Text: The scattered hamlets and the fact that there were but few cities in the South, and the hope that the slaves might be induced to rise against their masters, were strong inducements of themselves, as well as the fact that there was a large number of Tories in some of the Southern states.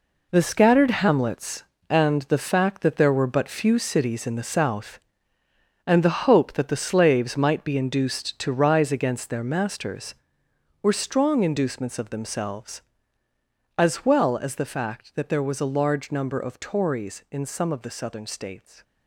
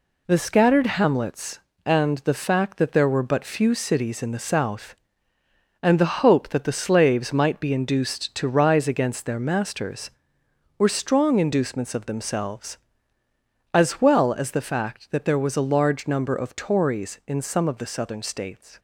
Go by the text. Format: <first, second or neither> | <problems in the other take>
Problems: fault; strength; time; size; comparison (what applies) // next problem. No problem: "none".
second | gets quieter; strong; throughout; 10 dB